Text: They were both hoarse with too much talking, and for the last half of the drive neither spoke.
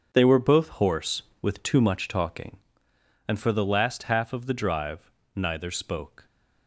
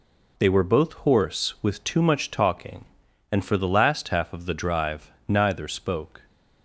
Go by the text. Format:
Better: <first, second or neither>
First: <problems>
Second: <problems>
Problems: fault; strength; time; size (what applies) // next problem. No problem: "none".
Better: second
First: gets quieter; strong; throughout; 11.5 dB // pauses between "drive" and "neither"; slight; at 5.1 s; 0.24 s long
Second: pauses between "drive" and "neither"; slight; at 5.0 s; 0.20 s long